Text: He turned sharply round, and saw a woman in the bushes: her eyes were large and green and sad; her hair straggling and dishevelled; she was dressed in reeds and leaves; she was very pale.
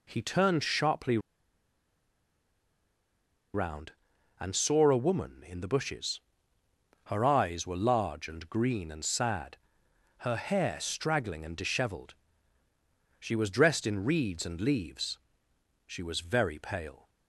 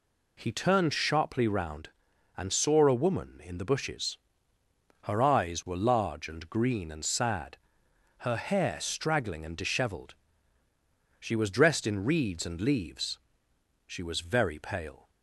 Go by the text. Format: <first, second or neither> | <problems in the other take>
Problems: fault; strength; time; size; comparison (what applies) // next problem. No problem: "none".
second | pauses between "sharply" and "round"; strong; at 1.1 s; 2.3 s long